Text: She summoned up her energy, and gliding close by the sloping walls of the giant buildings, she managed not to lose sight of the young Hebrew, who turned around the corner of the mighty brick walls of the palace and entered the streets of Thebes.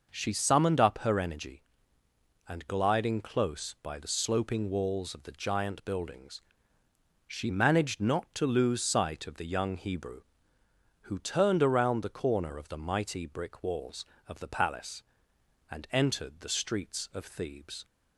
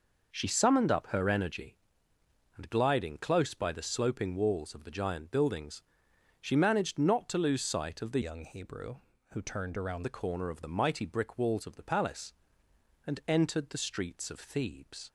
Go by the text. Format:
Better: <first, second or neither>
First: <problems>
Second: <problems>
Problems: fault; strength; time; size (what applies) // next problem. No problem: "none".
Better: first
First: none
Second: changes voice from "young" to "around"; from 8.2 to 10.0 s; 1.8 s long